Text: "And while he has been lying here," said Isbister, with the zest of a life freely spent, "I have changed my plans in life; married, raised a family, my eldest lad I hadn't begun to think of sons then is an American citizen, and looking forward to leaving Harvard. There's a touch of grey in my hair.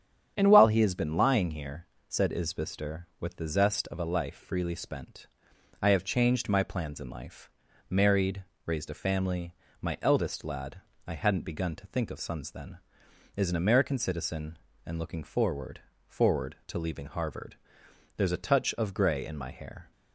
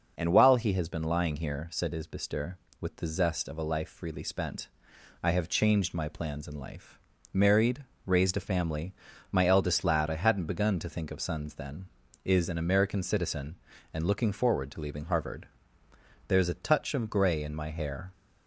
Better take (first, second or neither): second